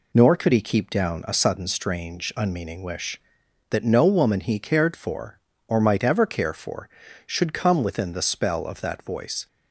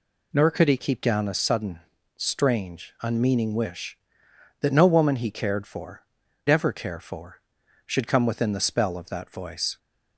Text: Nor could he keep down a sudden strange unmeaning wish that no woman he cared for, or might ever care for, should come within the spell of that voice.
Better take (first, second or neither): first